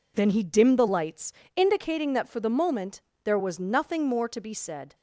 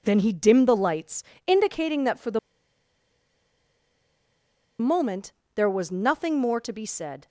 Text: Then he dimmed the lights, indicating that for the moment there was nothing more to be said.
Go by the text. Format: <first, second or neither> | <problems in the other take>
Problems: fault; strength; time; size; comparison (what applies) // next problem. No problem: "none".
first | pauses between "the" and "moment"; strong; at 2.3 s; 2.4 s long // pauses between "moment" and "there"; slight; at 5.3 s; 0.22 s long; slight in the first